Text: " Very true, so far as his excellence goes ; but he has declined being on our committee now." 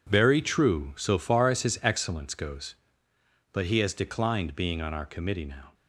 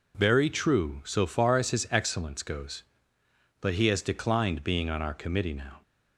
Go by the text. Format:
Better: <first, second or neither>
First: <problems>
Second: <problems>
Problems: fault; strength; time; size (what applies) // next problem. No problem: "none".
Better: second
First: gets quieter; strong; throughout; 11.5 dB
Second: none